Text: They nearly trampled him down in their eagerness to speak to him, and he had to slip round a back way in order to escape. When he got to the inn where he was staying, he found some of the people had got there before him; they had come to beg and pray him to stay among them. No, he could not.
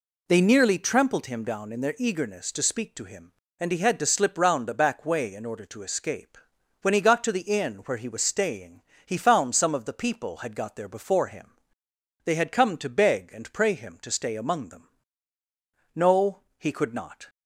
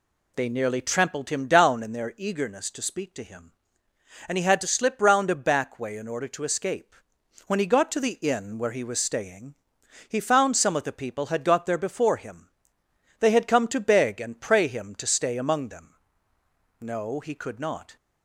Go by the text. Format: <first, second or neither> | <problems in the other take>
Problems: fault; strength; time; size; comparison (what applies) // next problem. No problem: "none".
neither | none